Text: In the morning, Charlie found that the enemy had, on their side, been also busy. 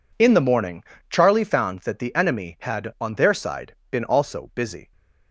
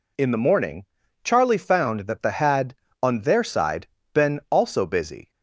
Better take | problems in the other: first | skips "enemy"; at 2.3 s

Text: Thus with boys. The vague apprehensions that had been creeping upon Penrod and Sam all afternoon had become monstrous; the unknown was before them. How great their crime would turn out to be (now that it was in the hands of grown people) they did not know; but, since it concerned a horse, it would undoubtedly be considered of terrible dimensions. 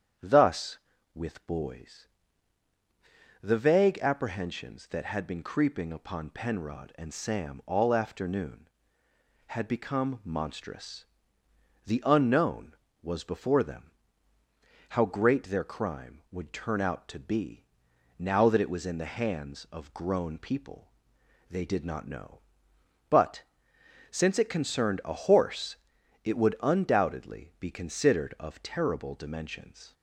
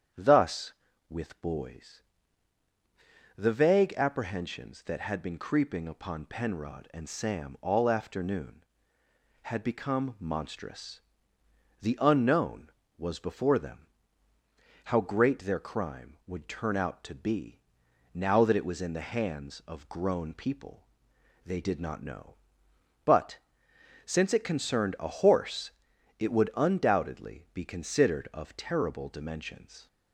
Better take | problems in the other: neither | starts louder than the rest; strong; the same in both

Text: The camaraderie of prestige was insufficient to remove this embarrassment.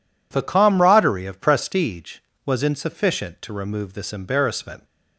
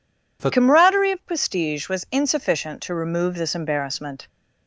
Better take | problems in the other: first | changes voice at "camaraderie"; from 0.5 s on; 3.7 s long

